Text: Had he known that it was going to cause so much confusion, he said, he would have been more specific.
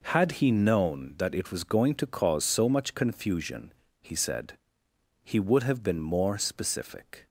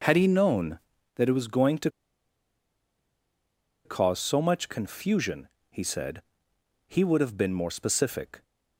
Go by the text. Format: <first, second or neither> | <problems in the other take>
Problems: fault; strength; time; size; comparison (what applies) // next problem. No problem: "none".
first | pauses between "to" and "cause"; strong; at 1.8 s; 1.9 s long